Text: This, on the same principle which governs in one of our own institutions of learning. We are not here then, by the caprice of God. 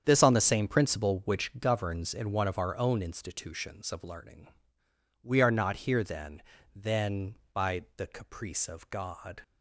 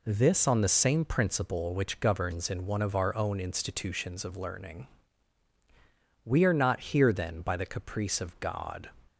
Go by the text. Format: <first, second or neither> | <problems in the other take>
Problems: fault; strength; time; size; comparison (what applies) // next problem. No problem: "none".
second | starts louder than the rest; strong; until 1.0 s; 8 dB // says "then" twice; at 6.7 s